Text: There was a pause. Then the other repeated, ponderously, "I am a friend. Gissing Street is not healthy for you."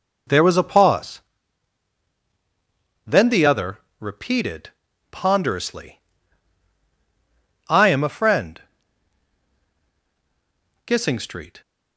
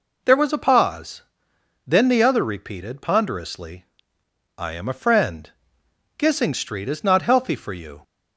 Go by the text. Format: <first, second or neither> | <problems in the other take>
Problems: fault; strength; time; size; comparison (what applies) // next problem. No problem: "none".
second | pauses between "other" and "repeated"; slight; at 3.7 s; 0.22 s long // stops before "is not healthy for you"; at 11.6 s